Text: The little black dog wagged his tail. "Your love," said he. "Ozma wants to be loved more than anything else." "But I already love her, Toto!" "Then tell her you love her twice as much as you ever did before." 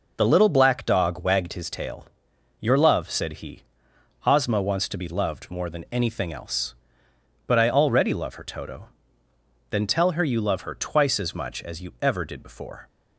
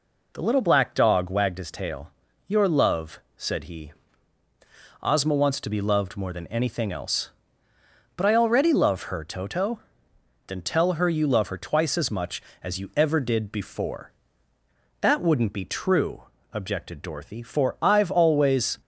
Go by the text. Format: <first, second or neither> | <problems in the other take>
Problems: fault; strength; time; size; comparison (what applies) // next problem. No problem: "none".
first | goes on to say "That wouldn't be true objected Dorothy for I've always"; strong; from 15.0 s on; 3.8 s long